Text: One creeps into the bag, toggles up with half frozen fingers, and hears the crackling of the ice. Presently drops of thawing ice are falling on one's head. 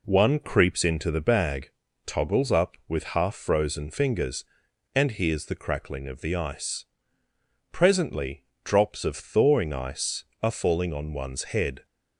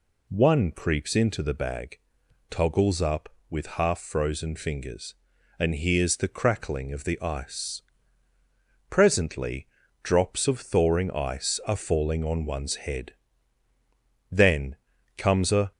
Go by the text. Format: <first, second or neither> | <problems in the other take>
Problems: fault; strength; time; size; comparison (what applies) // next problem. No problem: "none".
first | pauses between "Presently" and "drops"; slight; at 9.6 s; 0.36 s long; slight in the first // goes on to say "Then comes a"; from 14.2 s on; 1.4 s long